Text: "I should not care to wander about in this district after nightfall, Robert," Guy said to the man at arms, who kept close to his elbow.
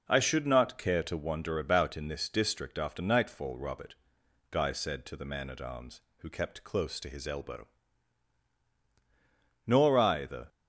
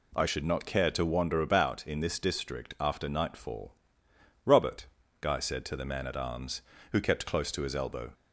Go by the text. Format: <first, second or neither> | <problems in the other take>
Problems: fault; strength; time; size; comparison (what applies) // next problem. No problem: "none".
second | goes on to say "Nor I the"; noticeable; from 9.6 s on; 0.84 s long